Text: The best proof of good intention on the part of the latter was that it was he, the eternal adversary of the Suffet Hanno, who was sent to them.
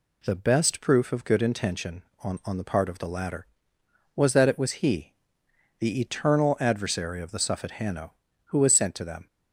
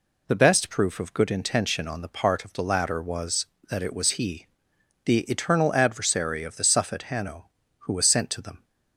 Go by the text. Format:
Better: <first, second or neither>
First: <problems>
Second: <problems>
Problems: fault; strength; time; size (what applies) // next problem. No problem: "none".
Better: second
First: says "on" twice; at 2.4 s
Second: none